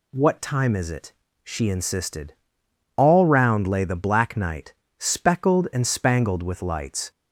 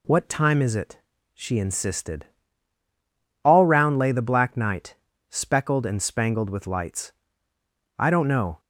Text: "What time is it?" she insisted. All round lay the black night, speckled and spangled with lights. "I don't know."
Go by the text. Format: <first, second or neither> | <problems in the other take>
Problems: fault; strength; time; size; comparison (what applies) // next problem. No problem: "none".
second | stops before "I don't know"; at 7.1 s